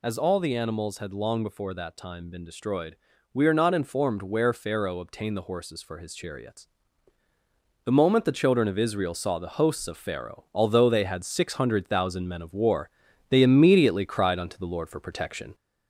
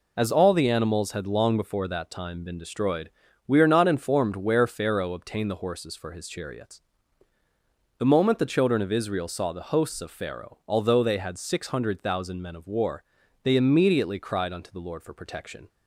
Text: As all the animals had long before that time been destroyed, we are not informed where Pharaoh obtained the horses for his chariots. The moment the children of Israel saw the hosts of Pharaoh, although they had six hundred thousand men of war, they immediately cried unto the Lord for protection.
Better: second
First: gets louder; slight; throughout; 2.5 dB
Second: none

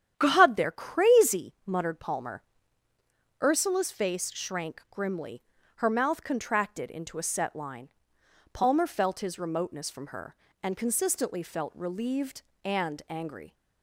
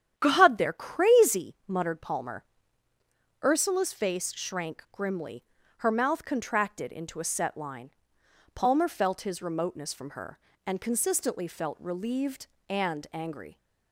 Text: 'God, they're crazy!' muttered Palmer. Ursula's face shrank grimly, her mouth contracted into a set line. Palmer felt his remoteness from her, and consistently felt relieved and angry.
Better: neither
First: starts louder than the rest; strong; until 1.1 s; 9.5 dB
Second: starts louder than the rest; strong; until 1.1 s; 9.5 dB

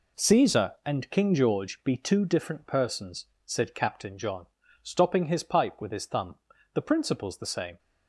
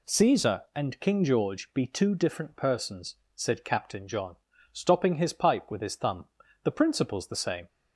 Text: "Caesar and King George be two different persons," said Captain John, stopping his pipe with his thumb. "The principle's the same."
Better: second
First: gets quieter; strong; throughout; 8 dB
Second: none

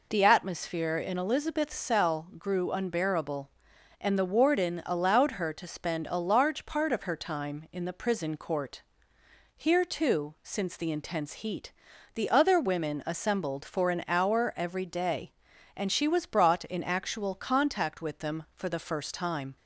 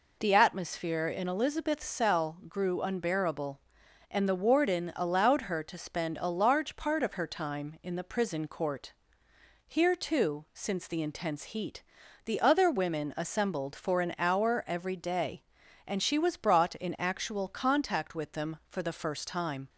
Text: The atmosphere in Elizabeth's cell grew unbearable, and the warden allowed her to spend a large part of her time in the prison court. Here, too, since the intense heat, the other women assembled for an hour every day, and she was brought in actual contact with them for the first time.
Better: neither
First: none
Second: none

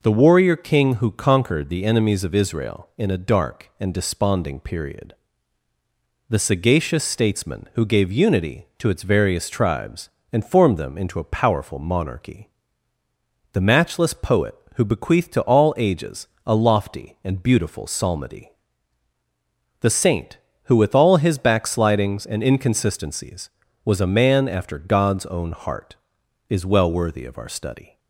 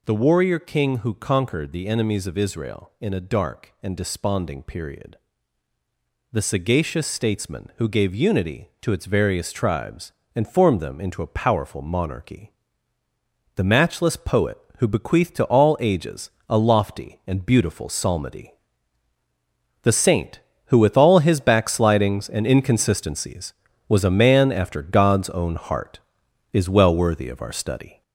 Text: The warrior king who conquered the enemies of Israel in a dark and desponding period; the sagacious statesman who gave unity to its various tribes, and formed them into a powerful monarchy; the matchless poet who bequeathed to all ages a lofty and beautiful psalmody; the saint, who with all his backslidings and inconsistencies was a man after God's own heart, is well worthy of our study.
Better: first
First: pauses between "ages" and "a"; slight; at 16.2 s; 0.22 s long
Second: gets louder; noticeable; throughout; 5 dB // pauses between "ages" and "a"; slight; at 16.2 s; 0.22 s long

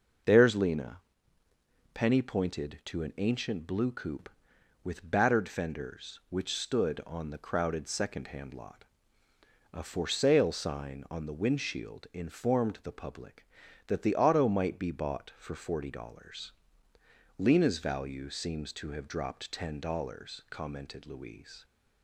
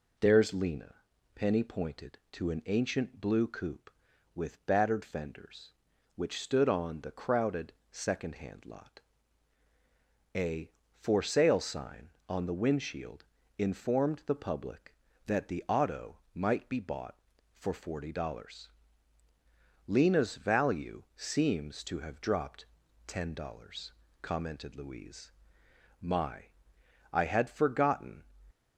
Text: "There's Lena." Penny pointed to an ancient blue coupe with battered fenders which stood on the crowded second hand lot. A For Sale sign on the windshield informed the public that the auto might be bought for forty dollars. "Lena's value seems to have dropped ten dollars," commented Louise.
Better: first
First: none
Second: pauses between "crowded" and "second"; slight; at 7.7 s; 0.20 s long // pauses between "windshield" and "informed"; slight; at 13.2 s; 0.34 s long // pauses between "auto" and "might"; slight; at 16.1 s; 0.16 s long // pauses between "dropped" and "ten"; at 22.6 s; 0.40 s long // goes on to say "My I had forgotten"; strong; from 26.0 s on; 2.2 s long

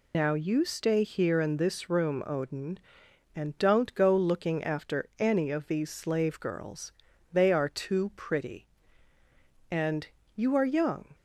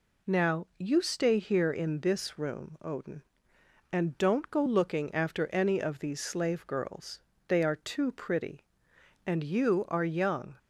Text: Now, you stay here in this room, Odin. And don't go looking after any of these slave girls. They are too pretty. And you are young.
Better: second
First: loses the start of "Now"; at 0.1 s; 115 ms // pauses between "And" and "you"; slight; at 10.0 s; 0.28 s long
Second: none

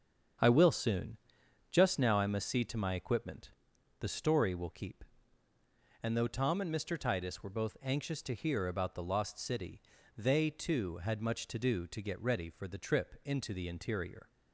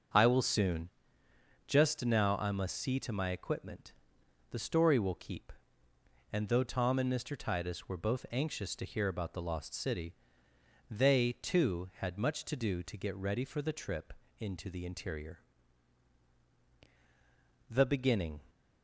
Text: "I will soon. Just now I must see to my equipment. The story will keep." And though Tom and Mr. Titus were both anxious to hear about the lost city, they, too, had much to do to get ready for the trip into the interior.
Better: first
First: starts louder than the rest; strong; until 1.9 s; 7.5 dB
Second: starts louder than the rest; until 1.9 s; 6.5 dB // pauses between "trip" and "into"; slight; at 14.1 s; 0.26 s long // goes on to say "The beginning"; noticeable; from 17.7 s on; 0.72 s long

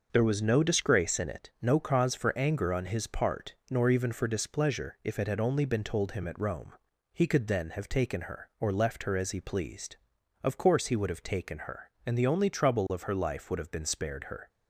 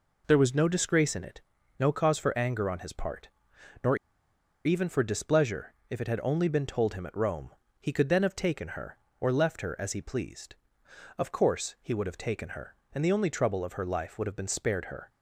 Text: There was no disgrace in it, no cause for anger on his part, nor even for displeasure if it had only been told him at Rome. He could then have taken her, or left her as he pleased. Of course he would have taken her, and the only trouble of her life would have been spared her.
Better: first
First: none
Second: pauses between "nor" and "even"; noticeable; at 3.9 s; 0.69 s long // pauses between "displeasure" and "if"; slight; at 5.7 s; 0.16 s long

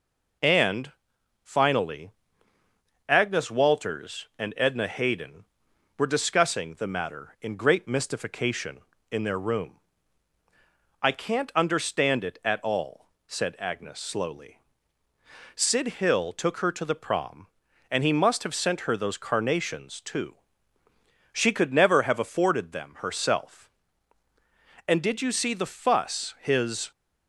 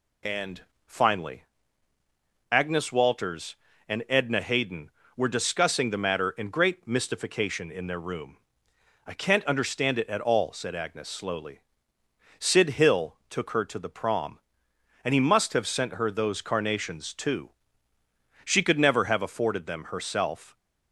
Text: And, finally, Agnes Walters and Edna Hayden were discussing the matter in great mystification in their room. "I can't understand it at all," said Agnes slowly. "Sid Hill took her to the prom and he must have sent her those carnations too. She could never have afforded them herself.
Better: second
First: goes on to say "And did you see the fuss his"; strong; from 24.8 s on; 2.0 s long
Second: none

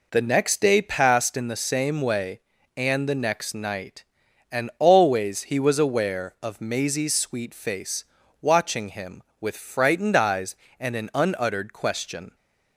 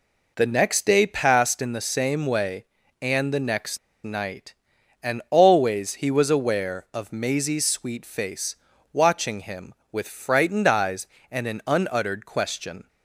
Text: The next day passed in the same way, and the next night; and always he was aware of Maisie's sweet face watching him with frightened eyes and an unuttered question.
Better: first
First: pauses between "face" and "watching"; slight; at 8.0 s; 0.36 s long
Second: pauses between "next" and "night"; slight; at 3.7 s; 0.25 s long // pauses between "face" and "watching"; slight; at 8.5 s; 0.36 s long

